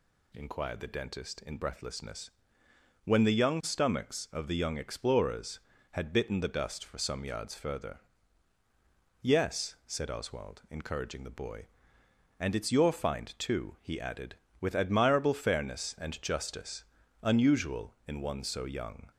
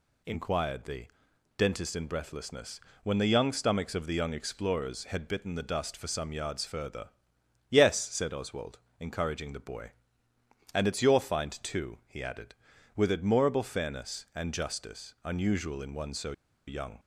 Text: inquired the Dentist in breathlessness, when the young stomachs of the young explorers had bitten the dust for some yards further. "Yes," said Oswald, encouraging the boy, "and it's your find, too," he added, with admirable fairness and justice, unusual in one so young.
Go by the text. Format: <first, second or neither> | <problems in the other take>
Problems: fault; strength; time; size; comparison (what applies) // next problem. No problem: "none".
first | pauses between "the" and "Dentist"; noticeable; at 1.0 s; 0.52 s long // pauses between "so" and "young"; slight; at 16.3 s; 0.34 s long